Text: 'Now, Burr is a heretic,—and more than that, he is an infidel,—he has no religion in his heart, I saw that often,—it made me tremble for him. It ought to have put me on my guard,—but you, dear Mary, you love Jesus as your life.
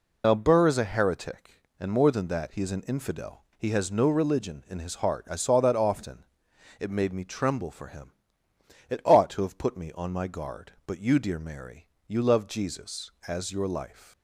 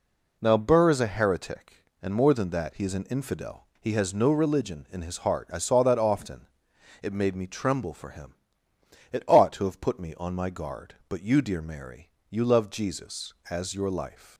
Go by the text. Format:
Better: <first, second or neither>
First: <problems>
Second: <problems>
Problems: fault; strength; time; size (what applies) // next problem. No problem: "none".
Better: second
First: loses the start of "Now"; at 0.2 s; 65 ms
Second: none